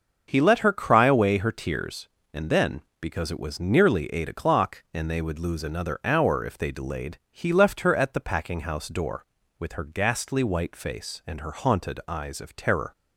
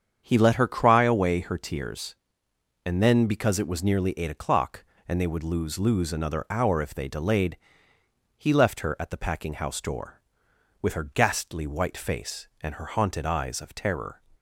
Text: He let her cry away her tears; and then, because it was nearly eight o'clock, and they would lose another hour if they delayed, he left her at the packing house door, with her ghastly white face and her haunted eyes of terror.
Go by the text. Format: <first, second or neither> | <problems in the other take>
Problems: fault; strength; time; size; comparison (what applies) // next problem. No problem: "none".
first | starts louder than the rest; strong; until 1.2 s; 7.5 dB; also in the first // says "lose" twice; at 5.7 s